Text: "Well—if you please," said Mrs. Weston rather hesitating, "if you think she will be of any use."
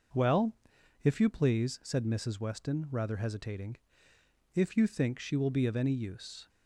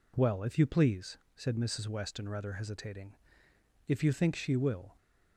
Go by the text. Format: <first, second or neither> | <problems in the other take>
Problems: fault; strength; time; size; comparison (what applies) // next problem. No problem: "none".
first | stops before "be of any use"; at 4.9 s